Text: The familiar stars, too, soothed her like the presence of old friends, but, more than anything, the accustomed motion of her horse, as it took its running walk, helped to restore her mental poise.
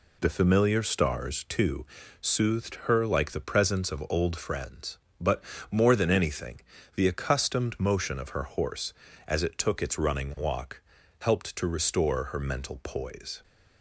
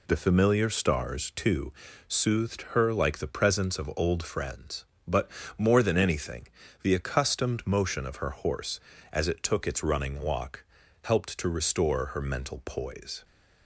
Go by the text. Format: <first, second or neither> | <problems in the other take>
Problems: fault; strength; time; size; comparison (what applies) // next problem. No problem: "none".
neither | none